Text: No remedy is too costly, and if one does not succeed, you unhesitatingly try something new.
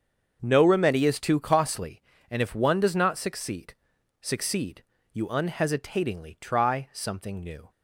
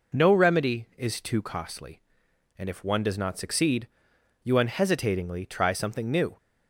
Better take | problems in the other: second | starts louder than the rest; until 1.4 s; 7 dB // says "succeed" twice; at 4.2 s

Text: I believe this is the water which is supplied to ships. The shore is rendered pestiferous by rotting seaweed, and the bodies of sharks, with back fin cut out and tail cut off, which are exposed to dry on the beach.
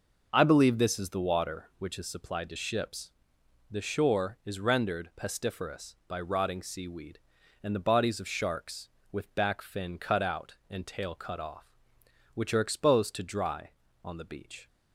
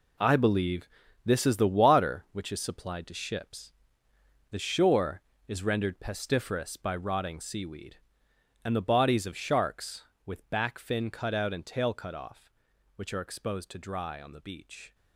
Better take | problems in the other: first | gets quieter; strong; throughout; 11 dB // pauses between "believe" and "this"; slight; at 0.8 s; 0.36 s long

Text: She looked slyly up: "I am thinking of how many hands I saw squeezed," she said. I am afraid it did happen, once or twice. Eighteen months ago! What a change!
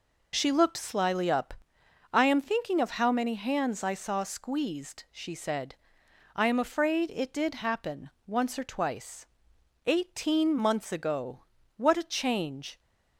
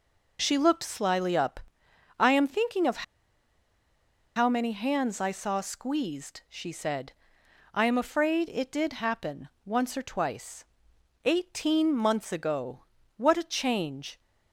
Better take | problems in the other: first | pauses between "of" and "how"; strong; at 3.0 s; 1.3 s long

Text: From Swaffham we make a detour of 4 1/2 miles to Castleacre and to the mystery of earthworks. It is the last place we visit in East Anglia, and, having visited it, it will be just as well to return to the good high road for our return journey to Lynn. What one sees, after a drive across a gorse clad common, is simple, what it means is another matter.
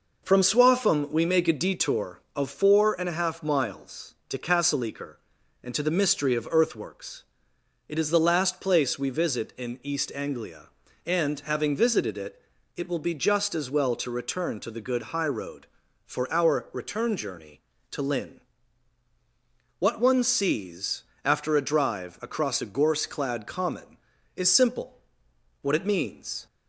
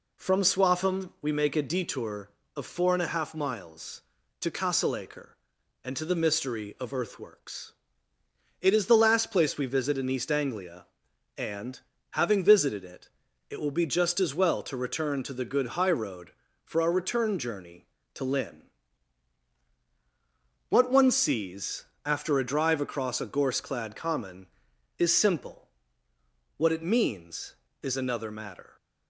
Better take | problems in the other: second | stops before "is another matter"; at 26.4 s

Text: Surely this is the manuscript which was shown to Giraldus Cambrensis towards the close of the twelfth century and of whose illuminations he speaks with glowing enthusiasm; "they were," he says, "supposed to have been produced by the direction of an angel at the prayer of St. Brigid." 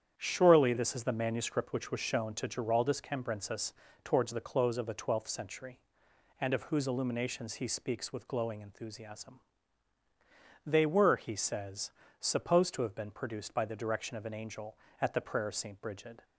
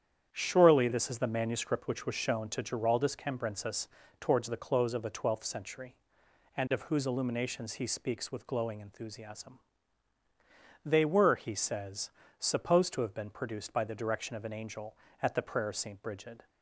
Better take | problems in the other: neither | starts louder than the rest; strong; the same in both // pauses between "Cambrensis" and "towards"; slight; the same in both

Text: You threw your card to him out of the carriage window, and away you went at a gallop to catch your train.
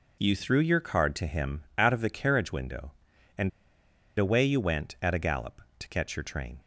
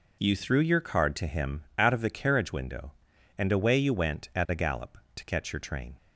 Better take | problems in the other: second | pauses between "him" and "out"; slight; at 1.6 s; 0.16 s long; slight in the second // pauses between "and" and "away"; noticeable; at 3.4 s; 0.69 s long

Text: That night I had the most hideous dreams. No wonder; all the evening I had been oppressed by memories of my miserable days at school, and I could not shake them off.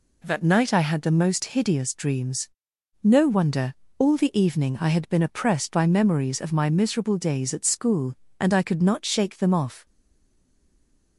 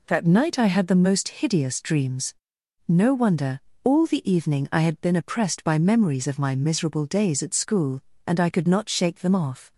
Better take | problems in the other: second | stays silent after the last word; noticeable; from 9.8 s on; 1.3 s long

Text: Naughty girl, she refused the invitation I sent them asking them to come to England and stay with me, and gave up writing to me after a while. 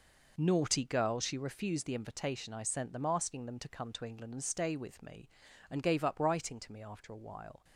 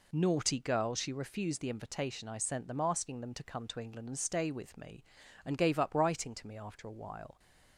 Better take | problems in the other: second | gets quieter; strong; throughout; 11 dB

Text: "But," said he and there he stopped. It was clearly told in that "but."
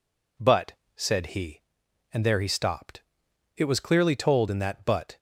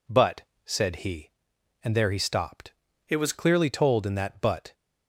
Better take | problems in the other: first | changes voice from "It" to "was"; from 3.1 to 3.3 s; 0.2 s long

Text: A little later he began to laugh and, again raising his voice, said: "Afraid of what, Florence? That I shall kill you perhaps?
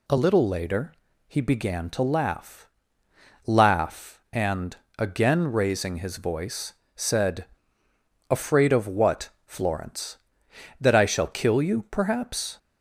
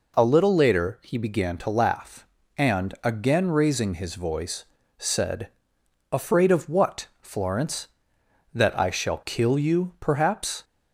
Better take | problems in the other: second | pauses between "later" and "he"; slight; at 0.9 s; 0.34 s long // says "laugh" twice; at 3.4 s

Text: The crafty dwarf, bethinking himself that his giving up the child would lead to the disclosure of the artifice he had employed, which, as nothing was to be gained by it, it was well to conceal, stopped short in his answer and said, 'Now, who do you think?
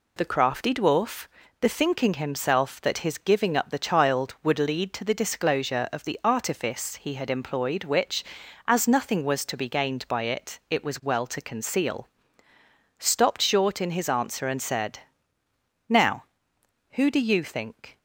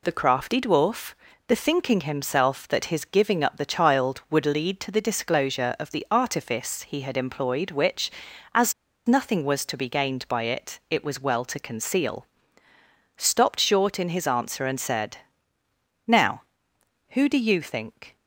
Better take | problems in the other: first | pauses between "as" and "nothing"; slight; at 8.7 s; 0.34 s long

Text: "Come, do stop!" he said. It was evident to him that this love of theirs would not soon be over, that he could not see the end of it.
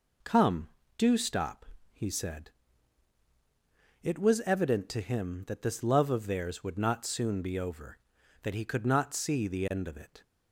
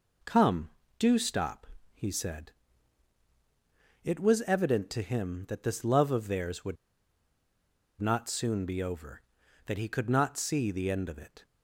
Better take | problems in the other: first | pauses between "would" and "not"; strong; at 6.7 s; 1.2 s long

